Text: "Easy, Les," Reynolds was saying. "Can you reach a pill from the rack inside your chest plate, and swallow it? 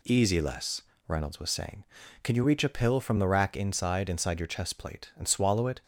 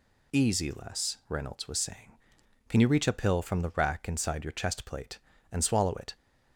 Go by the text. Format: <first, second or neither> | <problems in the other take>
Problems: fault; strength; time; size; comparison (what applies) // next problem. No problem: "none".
second | says "inside" twice; at 4.0 s